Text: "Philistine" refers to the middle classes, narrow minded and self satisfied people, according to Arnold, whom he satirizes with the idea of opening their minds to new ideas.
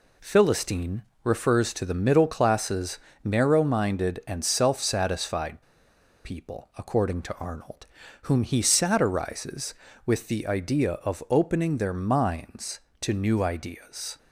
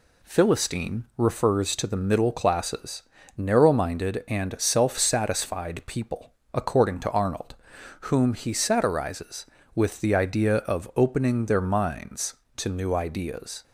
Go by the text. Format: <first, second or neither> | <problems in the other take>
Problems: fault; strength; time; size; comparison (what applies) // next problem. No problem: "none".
second | pauses between "Philistine" and "refers"; slight; at 1.0 s; 0.22 s long // pauses between "satisfied" and "people"; noticeable; at 5.6 s; 0.62 s long